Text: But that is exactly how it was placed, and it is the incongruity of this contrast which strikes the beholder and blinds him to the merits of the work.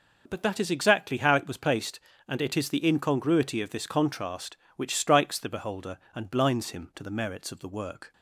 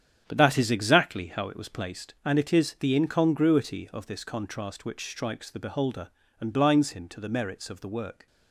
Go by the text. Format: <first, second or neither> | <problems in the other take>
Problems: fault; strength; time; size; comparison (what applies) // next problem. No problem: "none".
first | starts louder than the rest; strong; until 2.1 s; 9 dB